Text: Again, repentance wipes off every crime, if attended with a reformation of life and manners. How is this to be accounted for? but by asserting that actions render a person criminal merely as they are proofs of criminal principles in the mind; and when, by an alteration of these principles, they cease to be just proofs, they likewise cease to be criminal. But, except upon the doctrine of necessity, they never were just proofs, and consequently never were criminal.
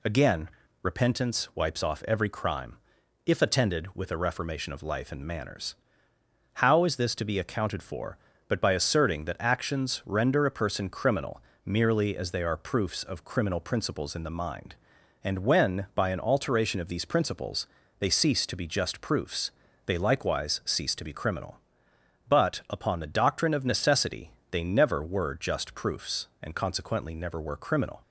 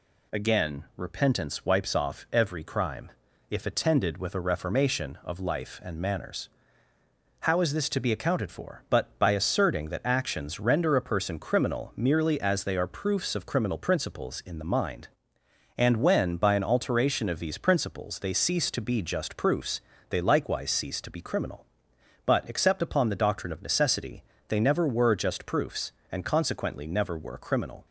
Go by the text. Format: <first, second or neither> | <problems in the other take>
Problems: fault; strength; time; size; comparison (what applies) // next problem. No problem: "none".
second | pauses between "criminal" and "merely"; slight; at 11.4 s; 0.24 s long // skips "except"; at 22.6 s